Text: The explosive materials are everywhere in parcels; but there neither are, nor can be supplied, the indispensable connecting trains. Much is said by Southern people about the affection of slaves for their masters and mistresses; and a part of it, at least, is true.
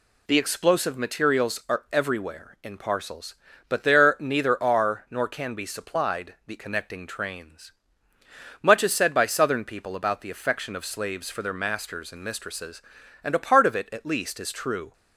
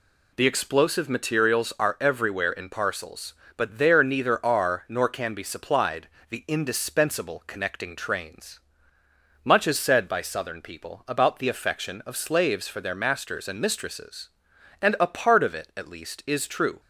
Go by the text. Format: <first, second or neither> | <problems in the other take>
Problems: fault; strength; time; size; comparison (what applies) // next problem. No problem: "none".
second | skips "indispensable"; at 6.5 s